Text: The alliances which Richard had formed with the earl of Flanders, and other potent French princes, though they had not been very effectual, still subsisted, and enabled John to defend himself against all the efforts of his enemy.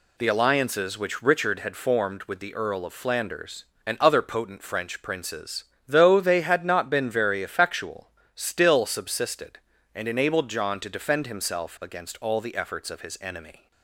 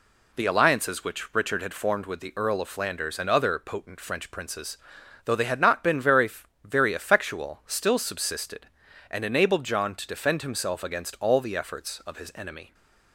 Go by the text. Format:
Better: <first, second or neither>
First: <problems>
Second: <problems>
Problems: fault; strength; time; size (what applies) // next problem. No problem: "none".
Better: first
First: none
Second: says "very" twice; at 6.6 s